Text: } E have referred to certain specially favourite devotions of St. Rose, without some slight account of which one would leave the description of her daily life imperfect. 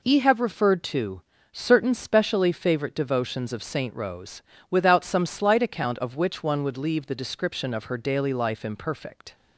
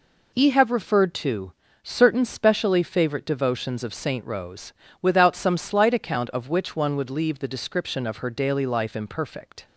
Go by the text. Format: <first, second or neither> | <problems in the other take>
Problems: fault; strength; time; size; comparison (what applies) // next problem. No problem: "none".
neither | pauses between "to" and "certain"; slight; the same in both